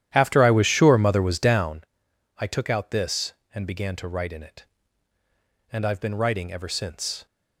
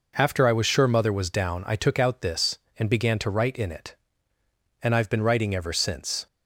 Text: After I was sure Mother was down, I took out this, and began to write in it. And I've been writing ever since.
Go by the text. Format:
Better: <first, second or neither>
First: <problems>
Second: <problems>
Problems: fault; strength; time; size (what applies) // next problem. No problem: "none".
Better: second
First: starts louder than the rest; strong; until 1.8 s; 11 dB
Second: none